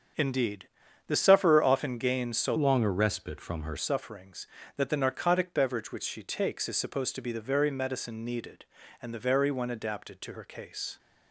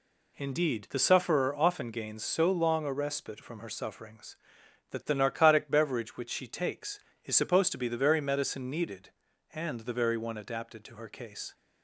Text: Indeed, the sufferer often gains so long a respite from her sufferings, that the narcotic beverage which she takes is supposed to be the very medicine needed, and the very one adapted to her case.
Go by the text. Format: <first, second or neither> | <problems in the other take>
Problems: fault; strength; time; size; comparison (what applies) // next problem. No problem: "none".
second | starts louder than the rest; strong; until 1.5 s; 7 dB // changes voice from "long" to "her"; from 2.5 to 3.7 s; 1.2 s long